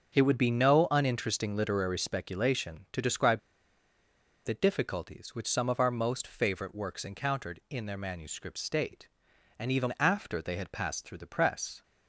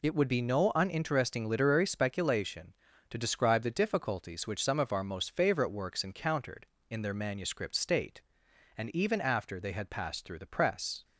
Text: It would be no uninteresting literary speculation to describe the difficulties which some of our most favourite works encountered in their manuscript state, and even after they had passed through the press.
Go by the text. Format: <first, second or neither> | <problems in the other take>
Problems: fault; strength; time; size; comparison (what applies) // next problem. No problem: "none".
second | starts louder than the rest; until 1.2 s; 6.5 dB // pauses between "describe" and "the"; at 3.3 s; 1.0 s long